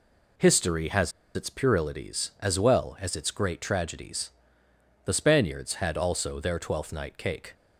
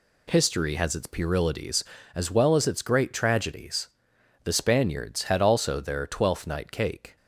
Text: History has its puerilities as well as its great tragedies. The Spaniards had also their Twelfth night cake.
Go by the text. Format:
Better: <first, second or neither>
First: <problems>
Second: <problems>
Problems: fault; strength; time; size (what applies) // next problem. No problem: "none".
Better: second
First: pauses between "has" and "its"; slight; at 1.1 s; 0.23 s long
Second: none